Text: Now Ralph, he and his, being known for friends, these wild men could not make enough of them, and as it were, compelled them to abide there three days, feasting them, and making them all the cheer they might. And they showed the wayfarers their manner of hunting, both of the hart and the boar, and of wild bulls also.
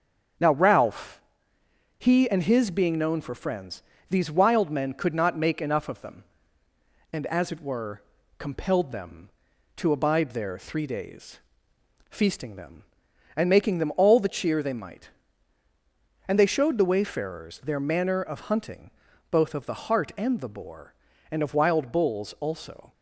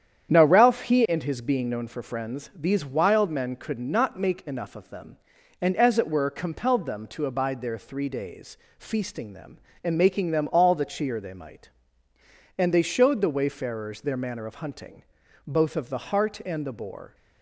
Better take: first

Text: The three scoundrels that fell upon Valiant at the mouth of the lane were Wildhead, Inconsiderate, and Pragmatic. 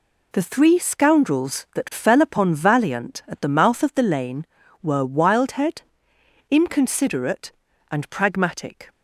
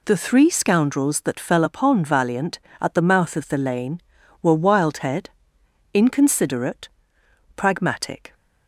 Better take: first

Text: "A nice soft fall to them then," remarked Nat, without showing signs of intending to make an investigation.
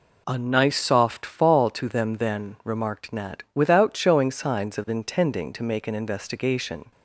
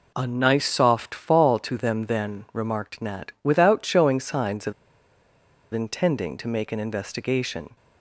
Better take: first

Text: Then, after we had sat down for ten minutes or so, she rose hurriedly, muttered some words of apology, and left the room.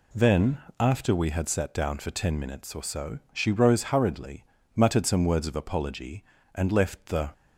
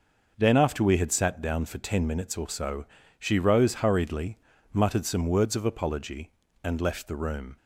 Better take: second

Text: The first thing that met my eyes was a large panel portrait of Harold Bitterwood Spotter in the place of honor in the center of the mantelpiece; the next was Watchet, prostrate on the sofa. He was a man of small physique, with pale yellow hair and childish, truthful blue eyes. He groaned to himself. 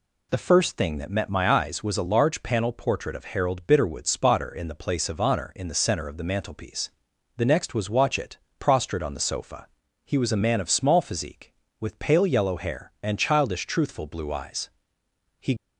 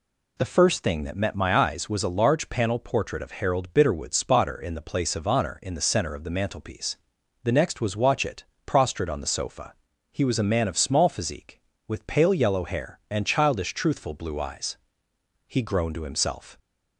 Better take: second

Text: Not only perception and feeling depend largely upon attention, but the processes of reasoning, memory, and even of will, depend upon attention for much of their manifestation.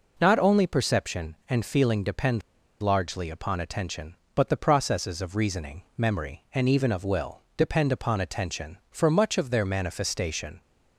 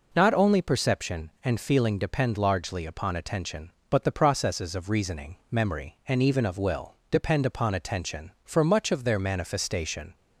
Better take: second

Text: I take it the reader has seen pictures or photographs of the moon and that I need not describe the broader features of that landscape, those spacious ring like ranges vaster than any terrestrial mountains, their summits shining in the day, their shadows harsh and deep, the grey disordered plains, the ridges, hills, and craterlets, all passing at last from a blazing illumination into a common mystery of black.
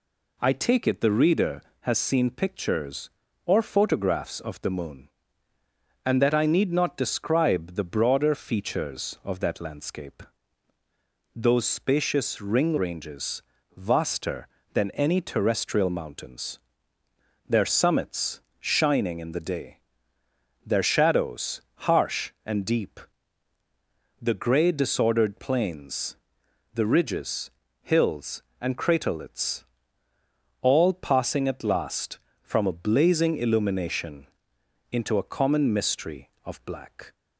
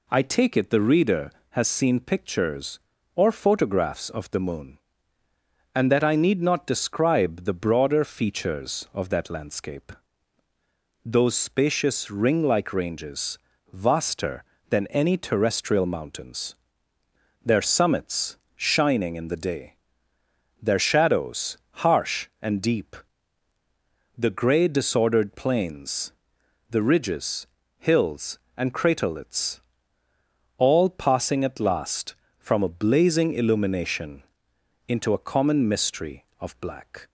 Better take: second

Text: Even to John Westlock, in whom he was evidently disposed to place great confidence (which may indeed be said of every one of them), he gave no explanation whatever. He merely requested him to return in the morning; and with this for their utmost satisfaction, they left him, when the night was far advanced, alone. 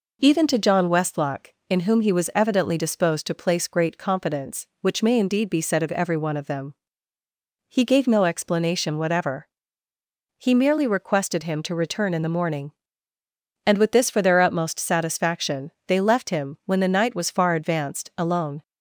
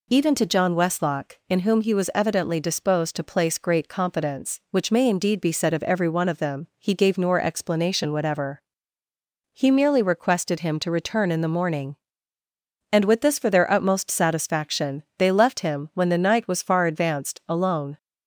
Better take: first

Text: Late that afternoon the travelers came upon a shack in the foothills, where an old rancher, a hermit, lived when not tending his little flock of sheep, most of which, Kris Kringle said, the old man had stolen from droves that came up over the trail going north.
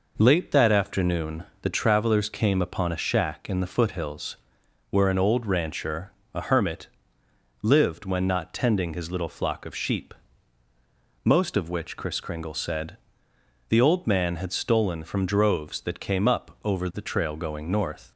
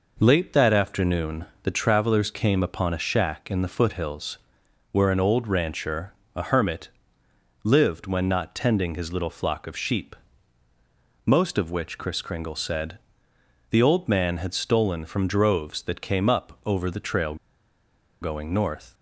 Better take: first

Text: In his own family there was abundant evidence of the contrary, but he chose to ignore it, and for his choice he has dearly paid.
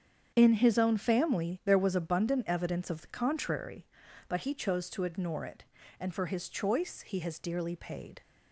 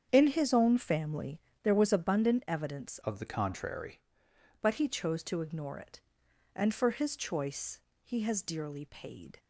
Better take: first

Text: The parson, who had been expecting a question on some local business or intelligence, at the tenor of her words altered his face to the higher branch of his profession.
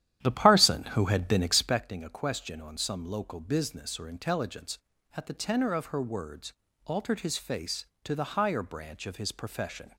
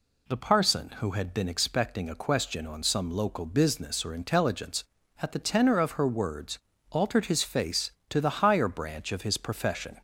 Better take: second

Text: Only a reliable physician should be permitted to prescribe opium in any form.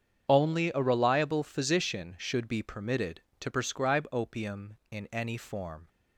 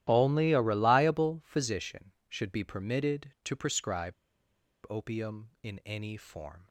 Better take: first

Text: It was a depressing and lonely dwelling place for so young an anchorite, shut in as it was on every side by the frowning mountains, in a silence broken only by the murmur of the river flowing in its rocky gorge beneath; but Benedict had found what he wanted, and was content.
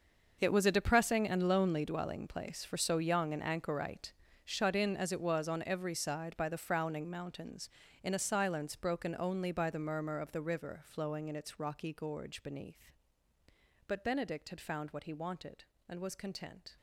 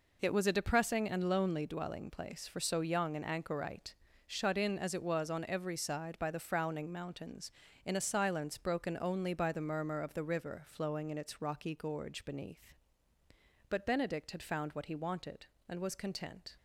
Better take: second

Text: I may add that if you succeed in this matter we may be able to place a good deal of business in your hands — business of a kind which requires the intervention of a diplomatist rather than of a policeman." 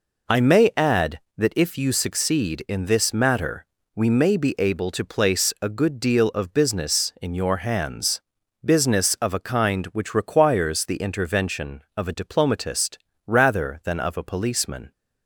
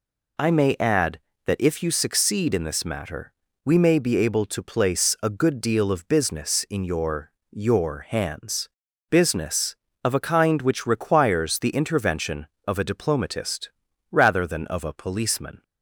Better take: first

